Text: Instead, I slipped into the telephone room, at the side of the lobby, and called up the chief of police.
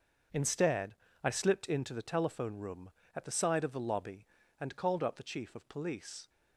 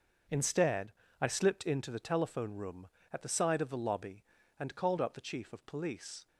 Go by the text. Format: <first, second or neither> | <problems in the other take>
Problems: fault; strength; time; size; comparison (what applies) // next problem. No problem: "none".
neither | starts louder than the rest; noticeable; the same in both